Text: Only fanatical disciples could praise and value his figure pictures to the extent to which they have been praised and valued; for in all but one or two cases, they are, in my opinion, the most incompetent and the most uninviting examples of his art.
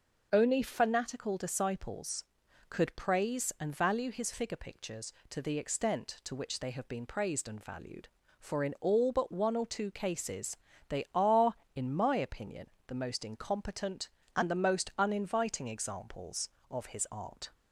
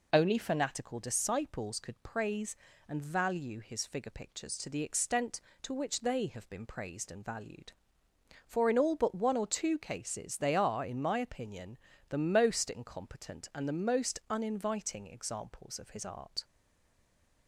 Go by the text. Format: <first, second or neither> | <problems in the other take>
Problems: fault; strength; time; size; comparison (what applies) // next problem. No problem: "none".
first | stays silent after the last word; from 16.4 s on; 1.0 s long